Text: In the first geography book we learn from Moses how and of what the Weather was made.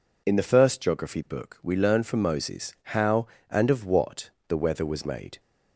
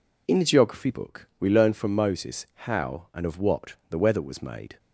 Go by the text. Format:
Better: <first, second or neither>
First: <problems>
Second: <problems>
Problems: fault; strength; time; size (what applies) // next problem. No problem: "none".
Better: first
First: pauses between "Moses" and "how"; slight; at 2.7 s; 0.22 s long // pauses between "what" and "the"; slight; at 4.2 s; 0.20 s long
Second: skips "first"; at 0.4 s // pauses between "Moses" and "how"; slight; at 2.4 s; 0.18 s long // pauses between "what" and "the"; slight; at 3.7 s; 0.16 s long